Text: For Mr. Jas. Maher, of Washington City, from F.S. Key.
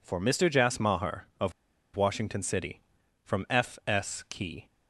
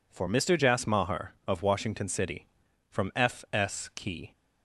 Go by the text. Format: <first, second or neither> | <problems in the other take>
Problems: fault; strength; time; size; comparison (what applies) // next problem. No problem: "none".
second | pauses between "of" and "Washington"; at 1.5 s; 0.42 s long